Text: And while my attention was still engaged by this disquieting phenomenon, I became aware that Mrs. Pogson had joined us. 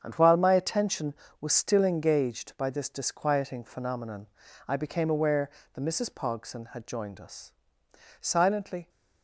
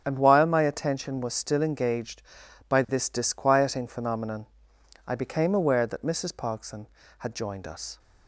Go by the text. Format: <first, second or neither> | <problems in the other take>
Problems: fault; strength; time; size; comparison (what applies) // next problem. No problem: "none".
second | starts louder than the rest; strong; until 1.0 s; 8 dB; strong in the second // goes on to say "Silently"; noticeable; from 8.2 s on; 0.68 s long